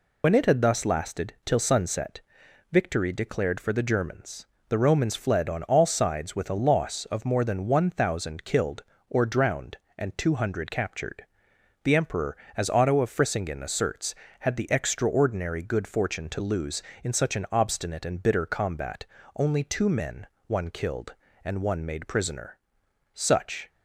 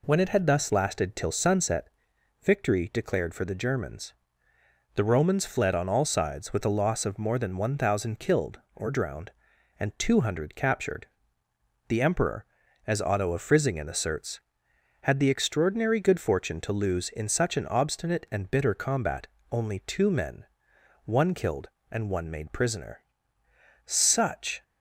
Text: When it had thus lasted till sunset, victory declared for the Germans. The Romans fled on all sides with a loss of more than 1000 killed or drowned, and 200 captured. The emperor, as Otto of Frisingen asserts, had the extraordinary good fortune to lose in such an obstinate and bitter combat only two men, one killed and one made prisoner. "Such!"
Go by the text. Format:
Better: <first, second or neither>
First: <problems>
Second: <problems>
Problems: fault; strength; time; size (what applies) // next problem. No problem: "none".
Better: second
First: loses the start of "When"; at 0.2 s; 55 ms // pauses between "combat" and "only"; slight; at 19.0 s; 0.32 s long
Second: pauses between "combat" and "only"; slight; at 19.2 s; 0.22 s long